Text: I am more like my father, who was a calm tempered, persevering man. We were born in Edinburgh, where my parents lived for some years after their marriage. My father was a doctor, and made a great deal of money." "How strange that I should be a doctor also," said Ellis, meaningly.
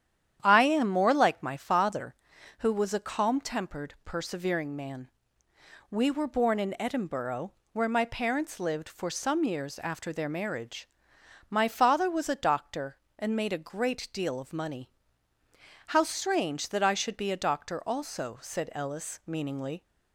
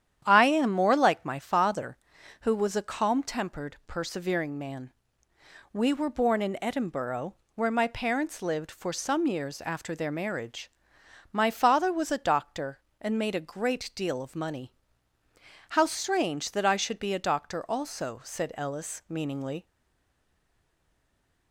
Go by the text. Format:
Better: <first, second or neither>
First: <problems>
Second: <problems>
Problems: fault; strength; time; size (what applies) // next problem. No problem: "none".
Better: first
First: starts louder than the rest; strong; until 1.4 s; 9.5 dB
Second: starts louder than the rest; strong; until 1.2 s; 9.5 dB // stays silent after the last word; noticeable; from 19.6 s on; 1.9 s long